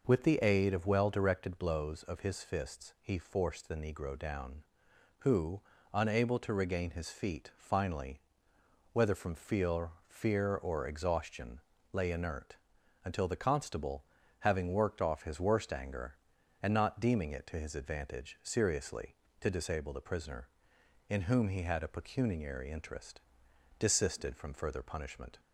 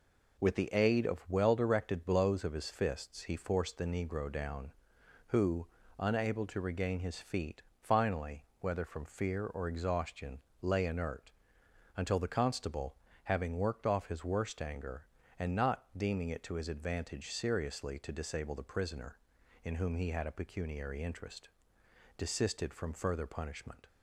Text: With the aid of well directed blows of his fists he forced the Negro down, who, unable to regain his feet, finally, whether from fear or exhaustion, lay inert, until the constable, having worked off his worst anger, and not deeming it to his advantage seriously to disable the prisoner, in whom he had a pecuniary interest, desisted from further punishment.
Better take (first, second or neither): second